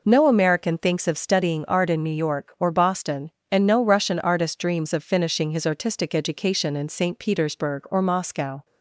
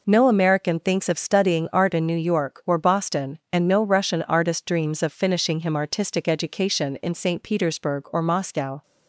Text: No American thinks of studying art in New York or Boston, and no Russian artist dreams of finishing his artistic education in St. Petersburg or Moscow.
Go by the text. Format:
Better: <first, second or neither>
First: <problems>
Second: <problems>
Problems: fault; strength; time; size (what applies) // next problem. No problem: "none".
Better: first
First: none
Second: says "him" for "his"; at 5.5 s